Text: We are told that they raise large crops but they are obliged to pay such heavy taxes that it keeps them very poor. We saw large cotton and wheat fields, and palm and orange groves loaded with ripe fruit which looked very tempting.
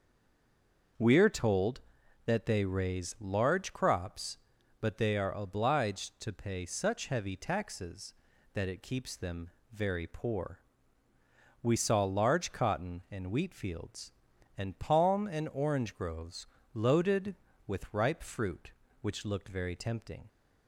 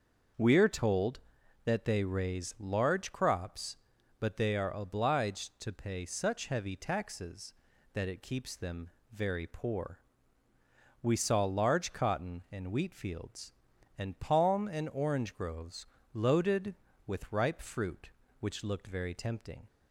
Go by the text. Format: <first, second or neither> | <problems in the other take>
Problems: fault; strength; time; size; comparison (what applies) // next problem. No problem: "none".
second | stays silent before the first word; until 0.9 s; 0.9 s long // starts louder than the rest; until 2.4 s; 6.5 dB; also in the second // pauses between "them" and "very"; slight; at 9.4 s; 0.24 s long; slight in the second // pauses between "groves" and "loaded"; slight; at 16.4 s; 0.28 s long; slight in the second